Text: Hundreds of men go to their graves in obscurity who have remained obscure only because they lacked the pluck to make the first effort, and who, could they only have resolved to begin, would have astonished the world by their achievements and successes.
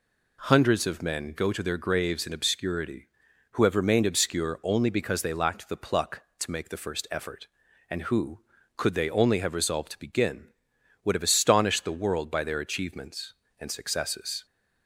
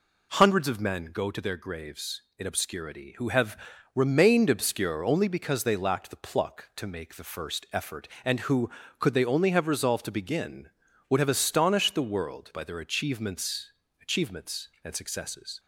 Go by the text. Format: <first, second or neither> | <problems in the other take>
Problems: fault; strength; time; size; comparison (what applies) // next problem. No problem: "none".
first | pauses between "have" and "remained"; at 3.5 s; 0.38 s long // says "achievements" twice; at 14.0 s